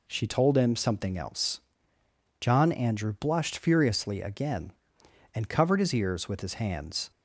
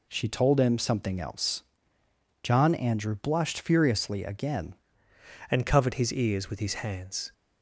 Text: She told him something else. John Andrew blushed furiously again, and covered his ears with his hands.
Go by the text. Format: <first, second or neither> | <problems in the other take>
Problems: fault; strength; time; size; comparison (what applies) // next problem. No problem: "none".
first | changes voice at "and"; from 5.5 s on; 1.8 s long